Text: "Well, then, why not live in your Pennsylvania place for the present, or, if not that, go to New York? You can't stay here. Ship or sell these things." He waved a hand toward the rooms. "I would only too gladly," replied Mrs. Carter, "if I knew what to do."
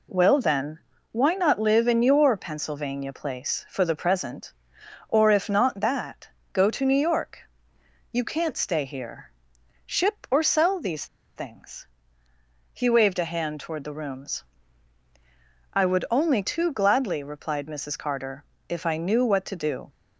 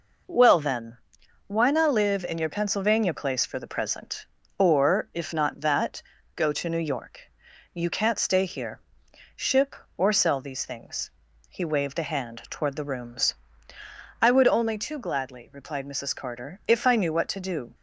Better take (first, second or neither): second